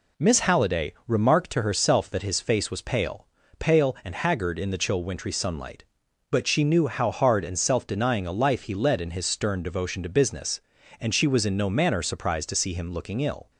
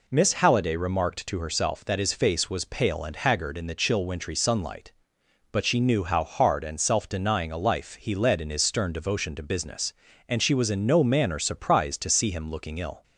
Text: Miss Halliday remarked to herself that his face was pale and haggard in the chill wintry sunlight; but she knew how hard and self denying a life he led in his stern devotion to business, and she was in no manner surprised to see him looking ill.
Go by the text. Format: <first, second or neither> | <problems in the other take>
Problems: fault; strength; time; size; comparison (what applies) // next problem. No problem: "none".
second | pauses between "Halliday" and "remarked"; slight; at 0.9 s; 0.16 s long // says "pale" twice; at 3.5 s